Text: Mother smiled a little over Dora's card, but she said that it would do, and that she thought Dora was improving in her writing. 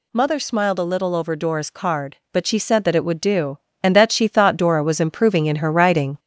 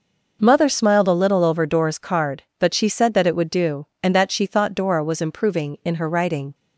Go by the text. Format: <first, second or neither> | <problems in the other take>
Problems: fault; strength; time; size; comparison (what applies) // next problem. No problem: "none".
second | gets louder; slight; throughout; 2.5 dB